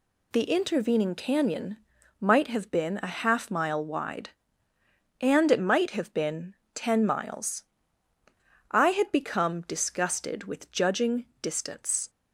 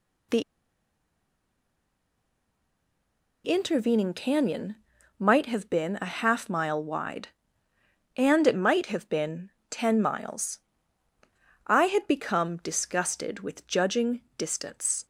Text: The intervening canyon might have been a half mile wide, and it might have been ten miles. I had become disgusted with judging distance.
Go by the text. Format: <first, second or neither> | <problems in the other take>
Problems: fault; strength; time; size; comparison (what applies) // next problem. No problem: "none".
first | pauses between "The" and "intervening"; strong; at 0.4 s; 3.0 s long // pauses between "canyon" and "might"; at 4.7 s; 0.44 s long; also in the first // pauses between "been" and "ten"; slight; at 9.5 s; 0.18 s long; slight in the first // pauses between "judging" and "distance"; slight; at 14.2 s; 0.16 s long; slight in the first